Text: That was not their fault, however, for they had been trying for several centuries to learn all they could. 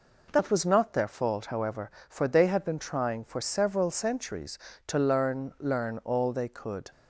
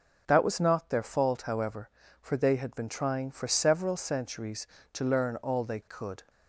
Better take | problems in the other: second | says "learn" twice; at 5.5 s

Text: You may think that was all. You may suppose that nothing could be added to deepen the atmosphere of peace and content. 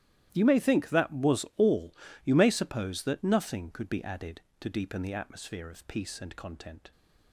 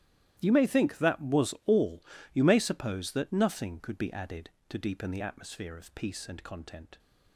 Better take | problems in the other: neither | starts louder than the rest; strong; the same in both

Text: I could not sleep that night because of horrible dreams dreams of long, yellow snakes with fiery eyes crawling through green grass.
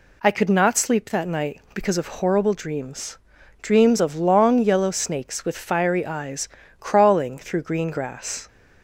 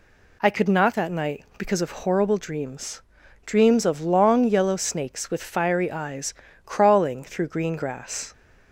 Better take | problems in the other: first | skips "sleep"; at 0.9 s // pauses between "dreams" and "dreams"; at 3.0 s; 0.42 s long; also in the first // pauses between "eyes" and "crawling"; slight; at 6.3 s; 0.32 s long; slight in the first

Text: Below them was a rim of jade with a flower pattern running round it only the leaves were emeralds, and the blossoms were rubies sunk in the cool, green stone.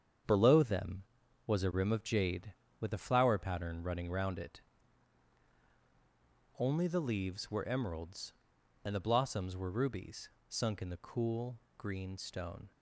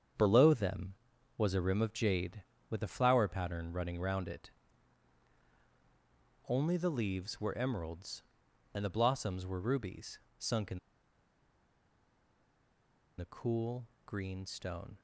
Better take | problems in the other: first | starts louder than the rest; strong; until 1.6 s; 7.5 dB; strong in the first // pauses between "it" and "only"; strong; at 4.5 s; 1.9 s long; strong in the first // pauses between "rubies" and "sunk"; slight; at 10.2 s; 0.18 s long; slight in the first // pauses between "in" and "the"; strong; at 10.7 s; 2.3 s long

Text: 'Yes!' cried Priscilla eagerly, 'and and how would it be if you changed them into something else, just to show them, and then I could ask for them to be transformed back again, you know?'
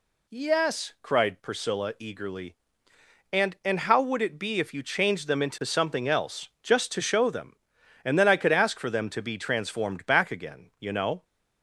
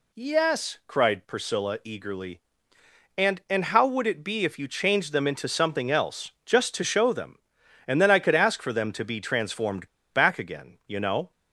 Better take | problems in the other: first | pauses between "transformed" and "back"; slight; at 9.8 s; 0.25 s long

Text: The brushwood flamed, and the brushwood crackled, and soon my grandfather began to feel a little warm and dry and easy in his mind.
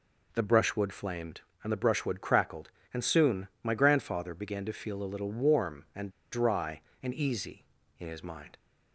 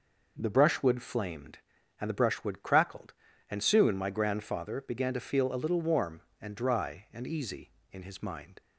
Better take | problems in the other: second | pauses between "and" and "dry"; slight; at 6.0 s; 0.22 s long

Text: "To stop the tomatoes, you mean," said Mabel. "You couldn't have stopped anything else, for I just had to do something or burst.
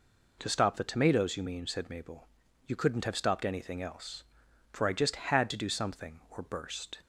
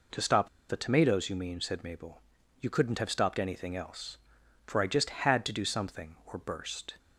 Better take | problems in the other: first | pauses between "stop" and "the"; slight; at 0.4 s; 0.22 s long

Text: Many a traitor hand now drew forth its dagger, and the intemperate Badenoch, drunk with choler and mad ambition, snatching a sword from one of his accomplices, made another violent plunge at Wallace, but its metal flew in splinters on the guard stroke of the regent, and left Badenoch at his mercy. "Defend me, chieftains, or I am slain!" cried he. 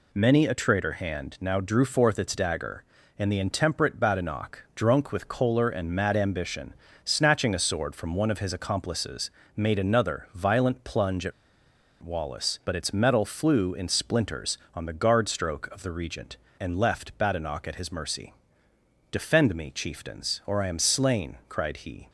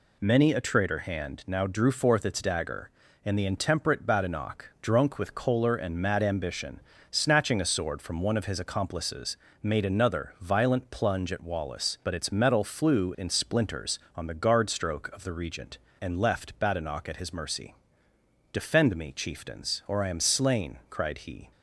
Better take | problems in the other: second | pauses between "at" and "Wallace"; noticeable; at 11.3 s; 0.70 s long

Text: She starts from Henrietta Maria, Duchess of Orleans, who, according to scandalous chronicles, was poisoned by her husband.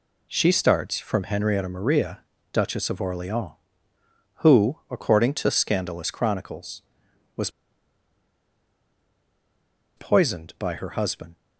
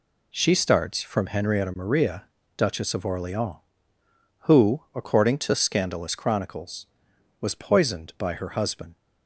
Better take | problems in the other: second | pauses between "was" and "poisoned"; strong; at 7.4 s; 2.4 s long

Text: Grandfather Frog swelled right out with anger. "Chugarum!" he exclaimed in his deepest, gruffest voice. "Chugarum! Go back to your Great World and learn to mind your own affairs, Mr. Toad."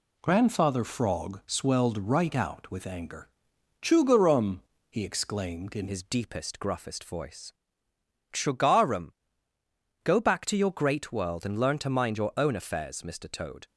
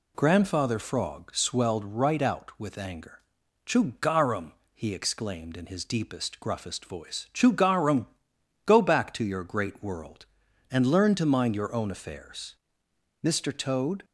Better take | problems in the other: second | changes voice at "his"; from 5.8 s on; 7.8 s long

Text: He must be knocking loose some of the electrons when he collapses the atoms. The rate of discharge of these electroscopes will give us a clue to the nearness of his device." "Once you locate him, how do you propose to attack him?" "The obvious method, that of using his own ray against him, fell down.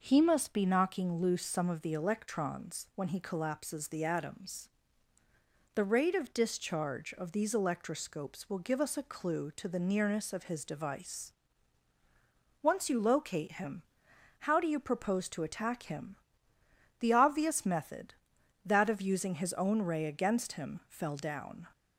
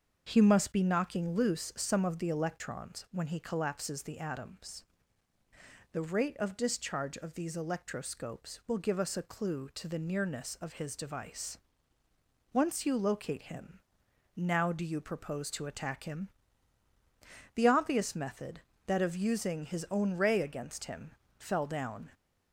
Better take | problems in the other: first | starts louder than the rest; until 1.2 s; 6.5 dB // says "now" for "how"; at 14.3 s

